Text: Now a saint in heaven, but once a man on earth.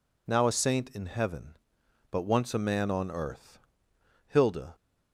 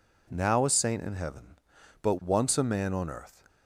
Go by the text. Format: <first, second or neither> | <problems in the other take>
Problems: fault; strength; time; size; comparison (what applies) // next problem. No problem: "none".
second | goes on to say "Hilda"; slight; from 4.2 s on; 0.48 s long